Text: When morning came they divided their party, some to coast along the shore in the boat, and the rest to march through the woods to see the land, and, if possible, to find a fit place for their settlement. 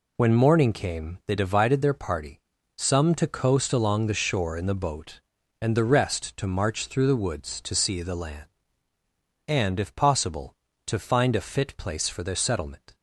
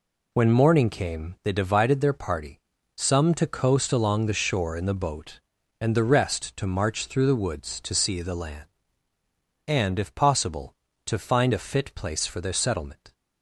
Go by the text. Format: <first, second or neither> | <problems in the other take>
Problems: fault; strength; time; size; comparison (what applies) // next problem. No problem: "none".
neither | none